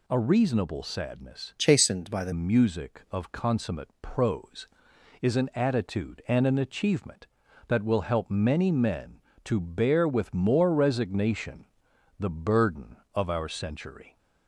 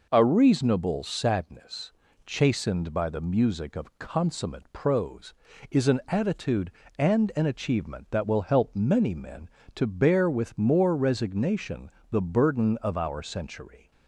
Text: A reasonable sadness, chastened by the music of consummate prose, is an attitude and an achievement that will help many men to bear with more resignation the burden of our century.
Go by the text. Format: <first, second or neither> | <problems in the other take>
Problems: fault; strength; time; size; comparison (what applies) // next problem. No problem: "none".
second | changes voice from "chastened" to "the"; from 1.5 to 2.3 s; 0.8 s long // pauses between "resignation" and "the"; noticeable; at 11.6 s; 0.56 s long; slight in the second